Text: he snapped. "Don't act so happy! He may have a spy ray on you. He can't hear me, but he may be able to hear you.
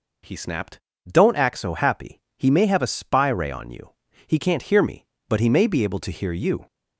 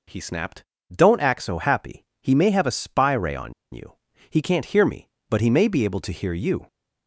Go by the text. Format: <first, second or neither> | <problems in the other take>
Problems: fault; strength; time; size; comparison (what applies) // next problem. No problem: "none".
first | pauses between "on" and "you"; slight; at 3.5 s; 0.20 s long